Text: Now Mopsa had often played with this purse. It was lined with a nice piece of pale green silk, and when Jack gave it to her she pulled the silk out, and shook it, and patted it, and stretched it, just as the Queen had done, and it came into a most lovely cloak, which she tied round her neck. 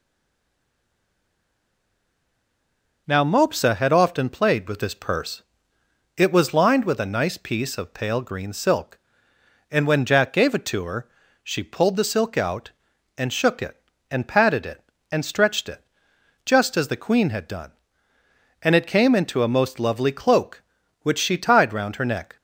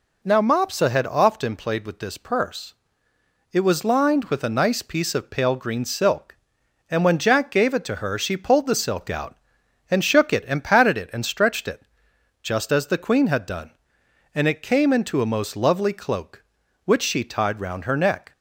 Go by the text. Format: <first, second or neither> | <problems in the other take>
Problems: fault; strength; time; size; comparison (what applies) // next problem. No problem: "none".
second | stays silent before the first word; strong; until 3.0 s; 3.0 s long // pauses between "her" and "she"; slight; at 11.0 s; 0.34 s long